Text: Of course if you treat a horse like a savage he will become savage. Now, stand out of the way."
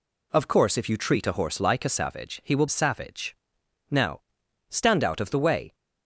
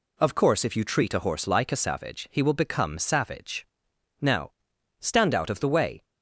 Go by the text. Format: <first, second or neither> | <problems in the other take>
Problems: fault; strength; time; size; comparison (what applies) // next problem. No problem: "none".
second | skips "become"; at 2.6 s